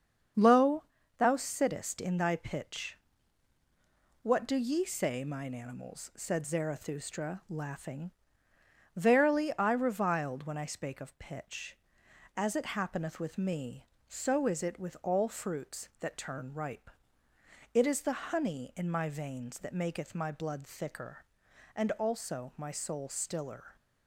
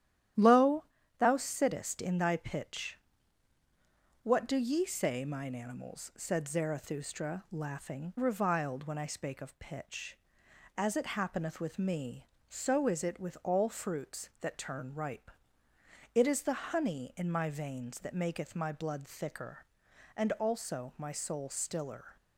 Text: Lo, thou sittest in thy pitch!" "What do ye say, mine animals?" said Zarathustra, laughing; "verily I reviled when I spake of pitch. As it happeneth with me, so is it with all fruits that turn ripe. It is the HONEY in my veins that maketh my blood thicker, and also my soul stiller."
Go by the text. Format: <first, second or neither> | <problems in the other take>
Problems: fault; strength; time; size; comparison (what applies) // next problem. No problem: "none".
first | starts louder than the rest; strong; until 1.7 s; 11.5 dB; strong in the first // skips "verily I"; at 8.1 s